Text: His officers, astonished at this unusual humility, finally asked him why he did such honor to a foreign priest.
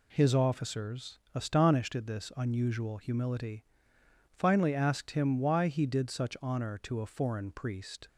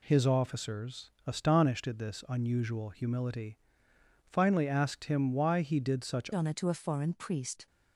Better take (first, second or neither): first